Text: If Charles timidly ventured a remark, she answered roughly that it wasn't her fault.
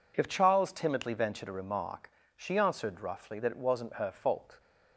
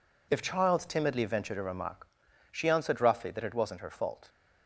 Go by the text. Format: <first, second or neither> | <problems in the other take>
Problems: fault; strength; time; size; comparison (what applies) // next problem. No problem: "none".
neither | none